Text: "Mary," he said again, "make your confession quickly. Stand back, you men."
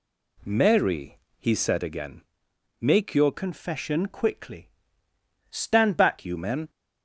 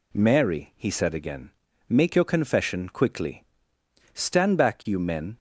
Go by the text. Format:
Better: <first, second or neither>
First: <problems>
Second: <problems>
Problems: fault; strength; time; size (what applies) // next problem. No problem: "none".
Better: second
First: changes voice from "confession" to "back"; from 3.3 to 6.2 s; 2.9 s long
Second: none